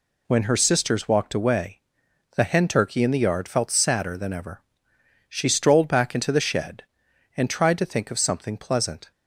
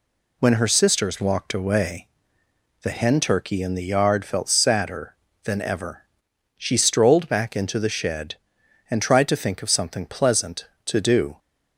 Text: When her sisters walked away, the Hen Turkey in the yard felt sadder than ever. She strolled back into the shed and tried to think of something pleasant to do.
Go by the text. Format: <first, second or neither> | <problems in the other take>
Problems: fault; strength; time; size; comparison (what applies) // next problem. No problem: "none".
second | stops before "to do"; at 9.1 s